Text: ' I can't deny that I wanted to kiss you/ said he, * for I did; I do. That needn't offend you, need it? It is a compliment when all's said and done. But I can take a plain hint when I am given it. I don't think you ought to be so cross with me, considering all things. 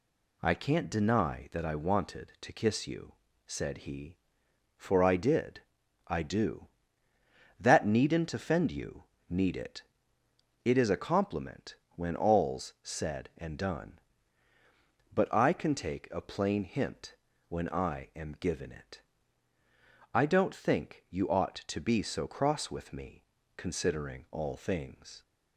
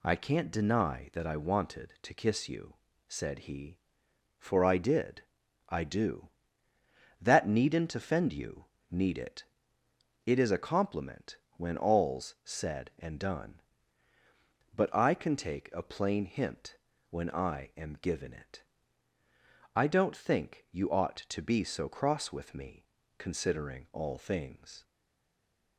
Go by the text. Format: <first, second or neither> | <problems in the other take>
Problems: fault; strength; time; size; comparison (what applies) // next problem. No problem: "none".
first | pauses between "compliment" and "when"; slight; at 11.3 s; 0.20 s long; slight in the first // pauses between "hint" and "when"; slight; at 16.7 s; 0.34 s long; slight in the first // stays silent after the last word; from 24.8 s on; 0.9 s long